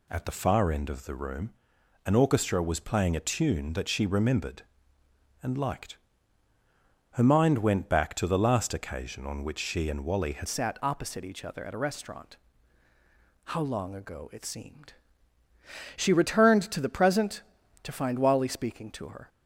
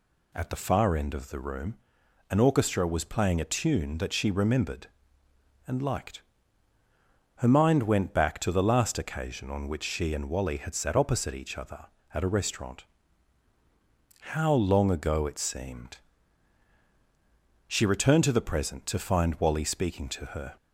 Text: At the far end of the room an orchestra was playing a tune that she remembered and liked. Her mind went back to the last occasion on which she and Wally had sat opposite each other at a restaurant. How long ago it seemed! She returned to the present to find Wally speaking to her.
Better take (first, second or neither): second